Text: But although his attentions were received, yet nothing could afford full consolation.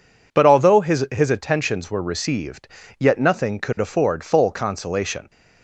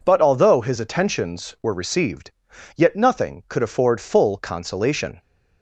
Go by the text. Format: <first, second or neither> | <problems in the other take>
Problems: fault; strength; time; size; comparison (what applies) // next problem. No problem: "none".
second | says "his" twice; at 1.0 s